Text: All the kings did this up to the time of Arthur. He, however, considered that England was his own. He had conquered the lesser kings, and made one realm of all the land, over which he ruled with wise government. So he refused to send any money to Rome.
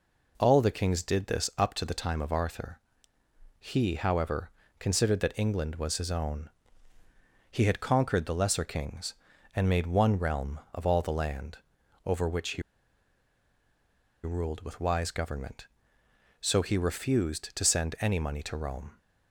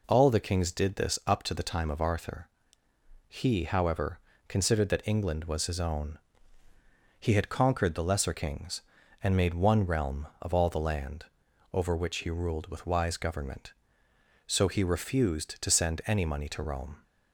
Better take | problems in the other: second | pauses between "he" and "ruled"; strong; at 12.6 s; 1.6 s long

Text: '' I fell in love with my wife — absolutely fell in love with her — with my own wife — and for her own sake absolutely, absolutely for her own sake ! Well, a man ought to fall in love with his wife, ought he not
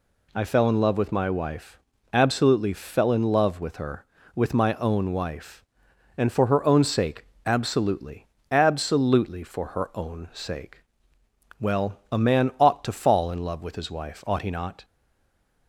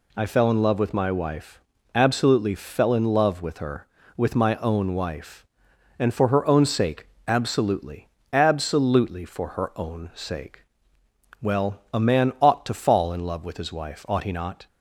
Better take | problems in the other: second | pauses between "sake" and "absolutely"; slight; at 7.2 s; 0.22 s long; slight in the second // stays silent after the last word; slight; from 14.8 s on; 0.8 s long

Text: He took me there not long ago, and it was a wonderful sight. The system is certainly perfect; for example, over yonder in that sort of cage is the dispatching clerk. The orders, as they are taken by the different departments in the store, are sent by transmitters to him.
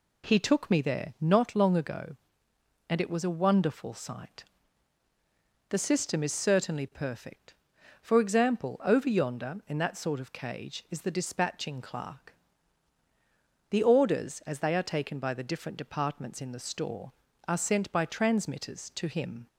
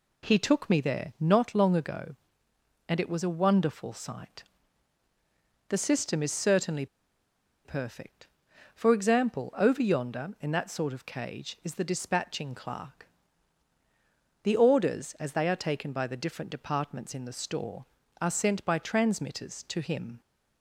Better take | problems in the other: first | pauses between "certainly" and "perfect"; noticeable; at 6.8 s; 0.78 s long

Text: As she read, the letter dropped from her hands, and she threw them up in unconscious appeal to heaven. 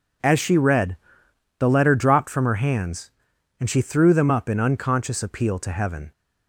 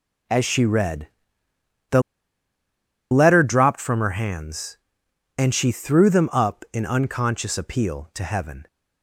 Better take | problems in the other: first | pauses between "the" and "letter"; at 2.0 s; 1.0 s long

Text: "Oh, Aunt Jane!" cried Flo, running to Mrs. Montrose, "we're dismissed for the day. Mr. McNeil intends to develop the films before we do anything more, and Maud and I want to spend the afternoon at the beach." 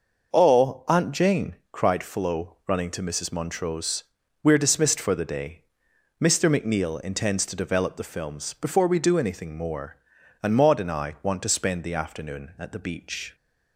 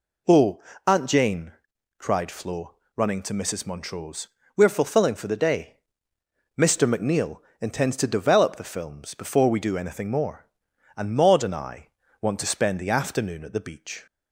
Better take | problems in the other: first | says "fulfilling" for "dismissed"; at 4.6 s // pauses between "McNeil" and "intends"; slight; at 7.3 s; 0.20 s long // pauses between "I" and "want"; slight; at 11.8 s; 0.34 s long

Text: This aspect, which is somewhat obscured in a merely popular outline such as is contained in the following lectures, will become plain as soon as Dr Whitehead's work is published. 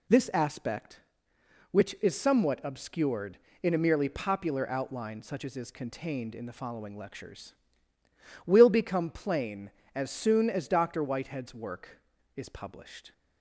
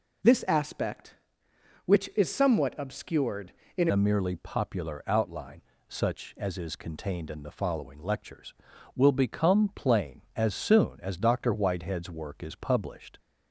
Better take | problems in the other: first | changes voice at "a"; from 3.9 s on; 9.2 s long // pauses between "outline" and "such"; slight; at 5.6 s; 0.26 s long

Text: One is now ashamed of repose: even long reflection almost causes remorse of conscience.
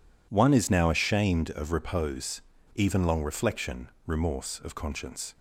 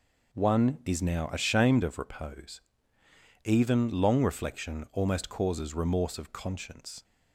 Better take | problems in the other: second | skips "almost causes"; at 3.9 s

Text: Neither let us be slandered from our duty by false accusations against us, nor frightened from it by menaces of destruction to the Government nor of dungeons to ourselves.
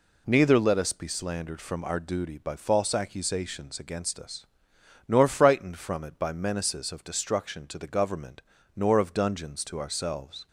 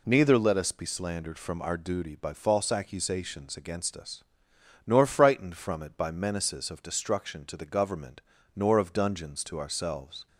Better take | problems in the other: neither | pauses between "Government" and "nor"; slight; the same in both

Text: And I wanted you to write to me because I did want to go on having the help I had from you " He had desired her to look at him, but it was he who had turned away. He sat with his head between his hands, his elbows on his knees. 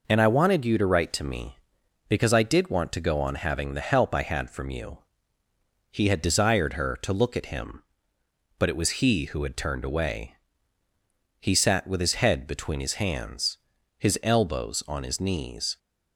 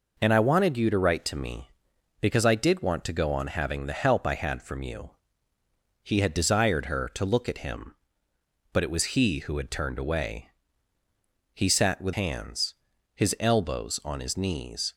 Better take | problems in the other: first | skips "his head between his"; at 12.1 s

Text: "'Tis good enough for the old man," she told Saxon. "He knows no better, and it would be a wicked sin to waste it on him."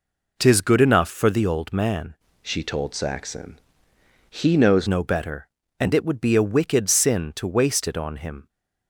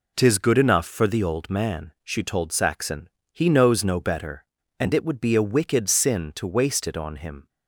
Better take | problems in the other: second | changes voice from "she" to "knows"; from 2.4 to 4.8 s; 2.4 s long

